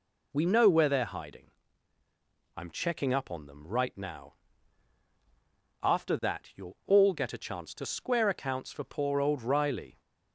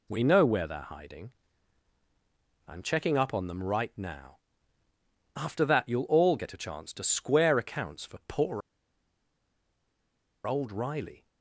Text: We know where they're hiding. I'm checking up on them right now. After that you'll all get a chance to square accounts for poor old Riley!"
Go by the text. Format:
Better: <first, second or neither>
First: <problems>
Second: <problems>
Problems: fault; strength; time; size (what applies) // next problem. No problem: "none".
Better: first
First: none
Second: pauses between "poor" and "old"; strong; at 8.6 s; 1.8 s long